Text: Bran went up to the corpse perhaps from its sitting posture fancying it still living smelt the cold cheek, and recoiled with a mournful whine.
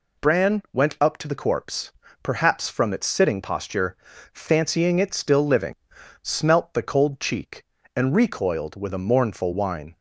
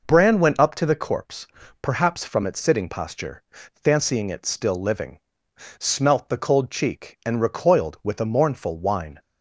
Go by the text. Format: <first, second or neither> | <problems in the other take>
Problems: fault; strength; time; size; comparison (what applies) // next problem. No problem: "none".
neither | pauses between "corpse" and "perhaps"; slight; the same in both // pauses between "posture" and "fancying"; slight; the same in both // pauses between "living" and "smelt"; noticeable; the same in both